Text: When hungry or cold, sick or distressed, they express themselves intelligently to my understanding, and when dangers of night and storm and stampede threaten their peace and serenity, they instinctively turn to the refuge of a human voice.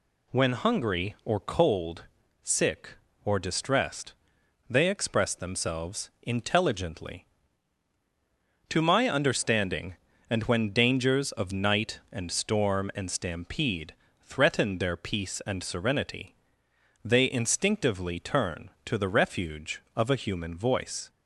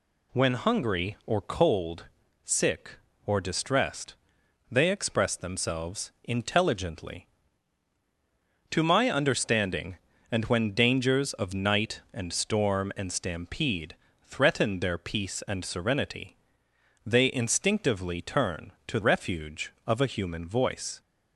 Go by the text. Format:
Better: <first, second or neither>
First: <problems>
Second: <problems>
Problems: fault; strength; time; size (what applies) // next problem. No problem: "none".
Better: first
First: pauses between "stampede" and "threaten"; slight; at 13.9 s; 0.26 s long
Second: pauses between "stampede" and "threaten"; slight; at 13.9 s; 0.26 s long // skips "the"; at 18.9 s